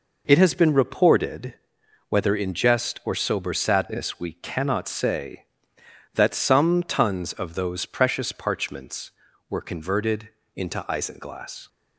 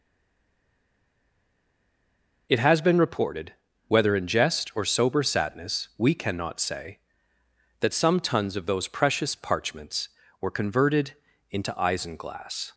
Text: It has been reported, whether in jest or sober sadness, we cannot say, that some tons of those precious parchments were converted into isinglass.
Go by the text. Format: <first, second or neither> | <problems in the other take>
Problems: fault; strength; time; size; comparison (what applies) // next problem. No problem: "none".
first | stays silent before the first word; until 2.4 s; 2.4 s long // pauses between "converted" and "into"; slight; at 11.1 s; 0.36 s long; slight in the first